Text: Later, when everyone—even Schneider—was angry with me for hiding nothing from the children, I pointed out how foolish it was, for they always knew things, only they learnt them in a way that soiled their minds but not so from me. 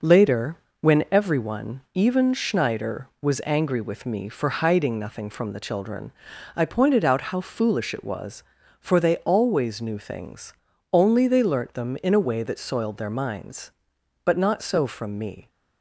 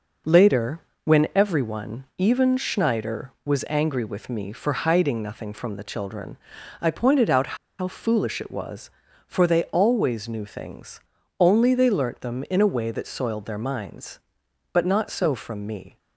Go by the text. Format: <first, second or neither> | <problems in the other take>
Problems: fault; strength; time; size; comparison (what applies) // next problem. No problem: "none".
first | pauses between "out" and "how"; slight; at 7.5 s; 0.22 s long